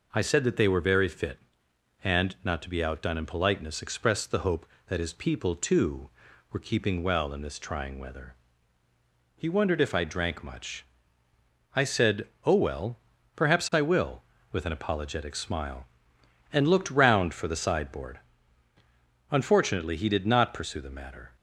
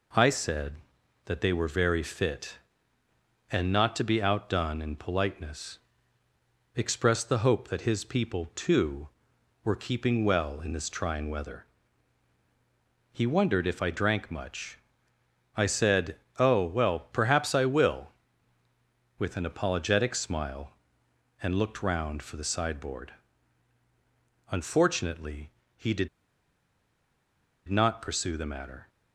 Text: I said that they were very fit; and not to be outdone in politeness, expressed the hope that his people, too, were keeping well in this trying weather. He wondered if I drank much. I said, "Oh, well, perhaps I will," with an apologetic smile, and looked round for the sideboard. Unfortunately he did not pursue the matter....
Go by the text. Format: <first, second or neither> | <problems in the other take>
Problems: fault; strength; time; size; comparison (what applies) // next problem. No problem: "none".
first | pauses between "Unfortunately" and "he"; slight; at 25.5 s; 0.26 s long // pauses between "did" and "not"; strong; at 26.0 s; 1.6 s long